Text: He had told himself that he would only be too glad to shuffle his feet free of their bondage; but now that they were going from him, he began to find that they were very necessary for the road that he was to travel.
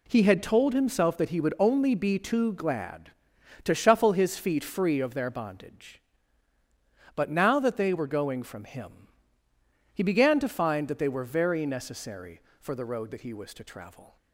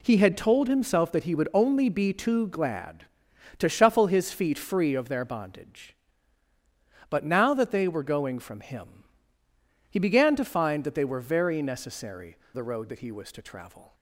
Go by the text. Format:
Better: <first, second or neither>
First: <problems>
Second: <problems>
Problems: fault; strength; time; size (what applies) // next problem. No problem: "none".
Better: first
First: none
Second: skips "for"; at 12.4 s